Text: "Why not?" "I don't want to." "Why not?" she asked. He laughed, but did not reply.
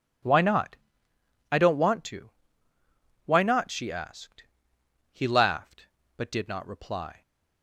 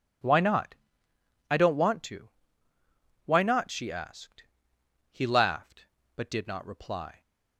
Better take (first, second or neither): neither